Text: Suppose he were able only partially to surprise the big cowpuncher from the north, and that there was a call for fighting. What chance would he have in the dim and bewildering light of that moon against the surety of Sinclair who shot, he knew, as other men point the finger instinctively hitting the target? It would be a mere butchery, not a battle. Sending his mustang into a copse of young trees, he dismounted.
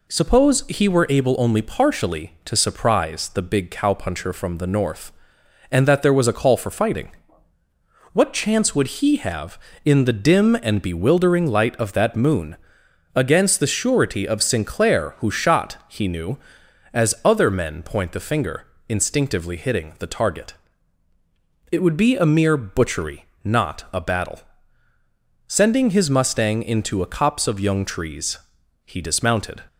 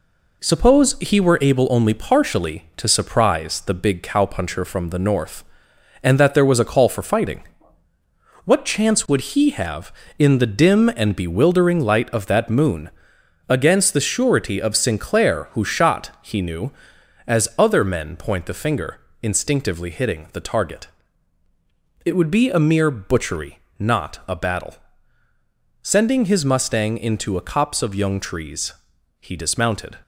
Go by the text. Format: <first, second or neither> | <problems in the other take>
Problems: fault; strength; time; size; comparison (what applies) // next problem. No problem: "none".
first | gets quieter; noticeable; throughout; 4.5 dB // pauses between "moon" and "against"; noticeable; at 12.9 s; 0.58 s long; noticeable in the first // pauses between "finger" and "instinctively"; slight; at 18.9 s; 0.24 s long; slight in the first